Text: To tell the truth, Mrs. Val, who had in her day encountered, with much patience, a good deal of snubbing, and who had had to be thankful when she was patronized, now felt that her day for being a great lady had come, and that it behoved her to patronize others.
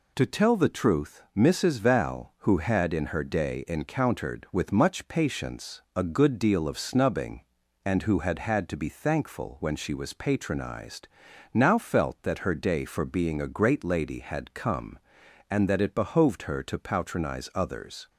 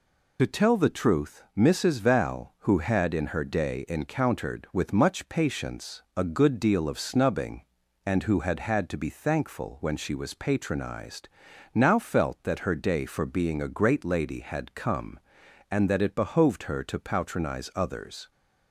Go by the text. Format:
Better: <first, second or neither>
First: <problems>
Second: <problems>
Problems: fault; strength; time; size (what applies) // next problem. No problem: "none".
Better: first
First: none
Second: loses the start of "To"; at 0.3 s; 35 ms